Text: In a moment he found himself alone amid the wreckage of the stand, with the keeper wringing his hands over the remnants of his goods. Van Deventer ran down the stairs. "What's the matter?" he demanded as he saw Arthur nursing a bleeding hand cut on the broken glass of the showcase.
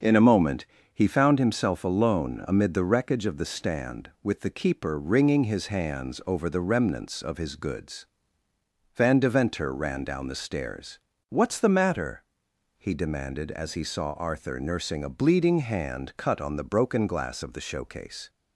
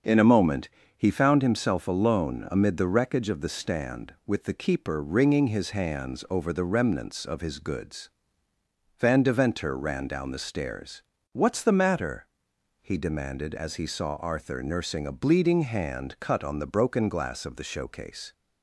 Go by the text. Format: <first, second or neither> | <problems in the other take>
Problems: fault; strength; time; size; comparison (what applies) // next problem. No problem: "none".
neither | starts louder than the rest; the same in both // pauses between "moment" and "he"; slight; the same in both